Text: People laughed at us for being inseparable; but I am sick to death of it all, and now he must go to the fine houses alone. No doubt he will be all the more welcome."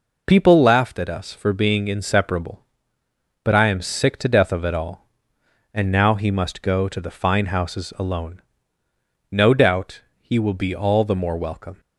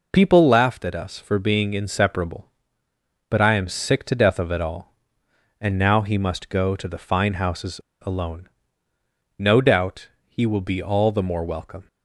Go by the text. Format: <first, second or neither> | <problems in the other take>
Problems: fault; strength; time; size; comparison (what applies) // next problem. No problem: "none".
first | pauses between "houses" and "alone"; slight; at 7.8 s; 0.23 s long // pauses between "doubt" and "he"; slight; at 10.0 s; 0.18 s long; slight in the first